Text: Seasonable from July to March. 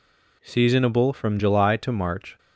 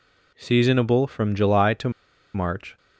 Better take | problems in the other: first | pauses between "to" and "March"; at 1.9 s; 0.43 s long

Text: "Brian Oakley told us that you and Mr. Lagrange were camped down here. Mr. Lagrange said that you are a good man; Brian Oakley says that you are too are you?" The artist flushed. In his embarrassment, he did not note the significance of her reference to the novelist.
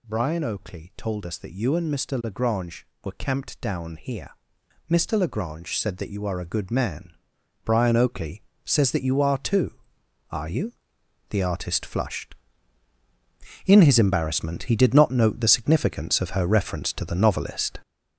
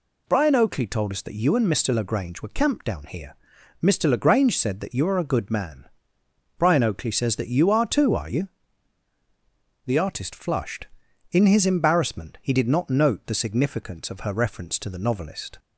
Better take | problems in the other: second | gets louder; throughout; 7 dB // pauses between "Oakley" and "says"; slight; at 8.4 s; 0.22 s long

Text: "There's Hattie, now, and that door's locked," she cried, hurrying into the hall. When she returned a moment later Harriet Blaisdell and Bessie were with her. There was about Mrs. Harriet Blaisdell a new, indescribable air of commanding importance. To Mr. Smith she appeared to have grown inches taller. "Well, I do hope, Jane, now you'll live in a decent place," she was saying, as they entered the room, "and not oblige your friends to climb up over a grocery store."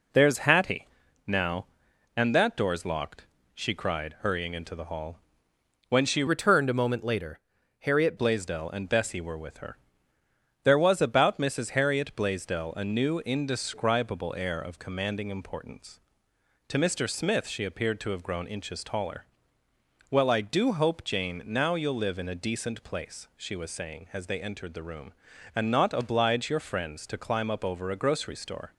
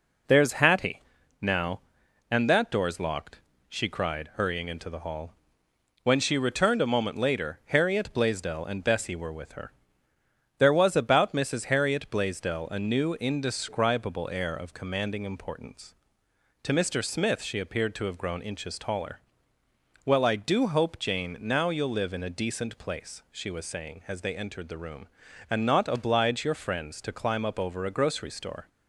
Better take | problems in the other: second | changes voice from "returned" to "Harriet"; from 6.2 to 8.1 s; 1.9 s long // pauses between "later" and "Harriet"; at 7.3 s; 0.42 s long

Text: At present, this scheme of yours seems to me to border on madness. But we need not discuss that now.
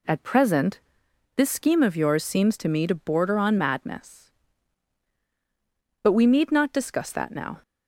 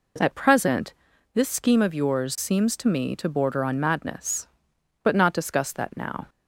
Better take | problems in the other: first | skips "we need"; at 5.1 s

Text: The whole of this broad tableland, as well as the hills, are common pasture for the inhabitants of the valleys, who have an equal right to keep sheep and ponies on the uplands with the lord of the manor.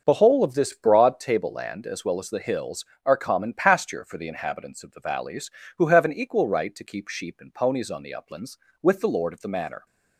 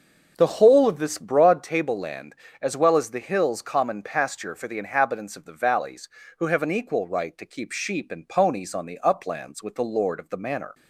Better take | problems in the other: first | starts louder than the rest; until 1.3 s; 6.5 dB; also in the first // skips "are"; at 3.6 s

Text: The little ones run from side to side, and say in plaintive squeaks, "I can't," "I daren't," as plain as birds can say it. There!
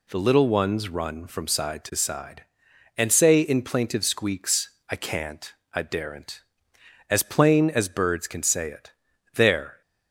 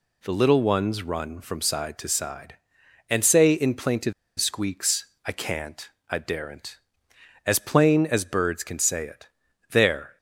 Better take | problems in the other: first | pauses between "plaintive" and "squeaks"; slight; at 4.1 s; 0.25 s long

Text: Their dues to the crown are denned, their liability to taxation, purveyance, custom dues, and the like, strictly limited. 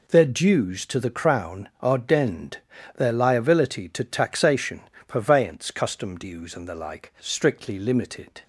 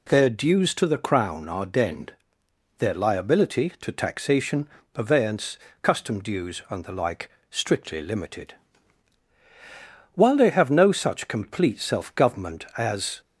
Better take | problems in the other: first | goes on to say "While they have no such complete self government as"; strong; from 10.1 s on; 3.0 s long

